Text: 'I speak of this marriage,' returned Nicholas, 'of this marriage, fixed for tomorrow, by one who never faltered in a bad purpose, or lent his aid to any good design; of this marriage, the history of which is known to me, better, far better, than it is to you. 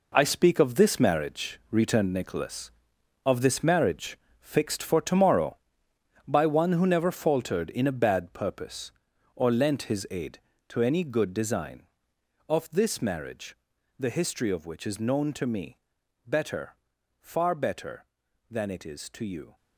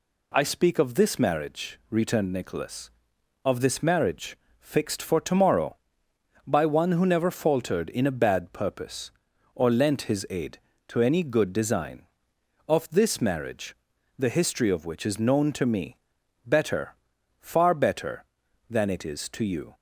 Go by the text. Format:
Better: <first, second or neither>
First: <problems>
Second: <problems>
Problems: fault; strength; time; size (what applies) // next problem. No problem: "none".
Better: second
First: gets quieter; strong; throughout; 10 dB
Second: none